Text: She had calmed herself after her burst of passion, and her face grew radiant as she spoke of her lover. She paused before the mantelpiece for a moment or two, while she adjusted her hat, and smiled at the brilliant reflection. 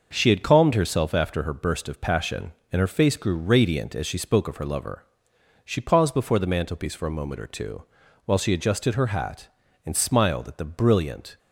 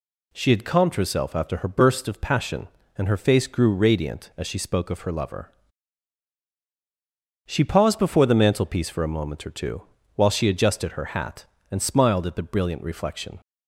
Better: second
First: stops before "reflection"; at 11.3 s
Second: none

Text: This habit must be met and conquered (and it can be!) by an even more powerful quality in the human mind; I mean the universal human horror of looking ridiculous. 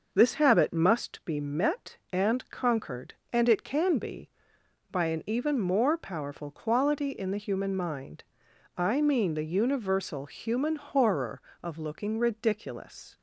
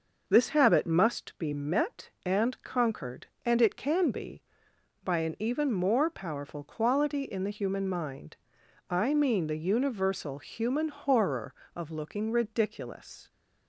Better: neither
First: none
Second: none

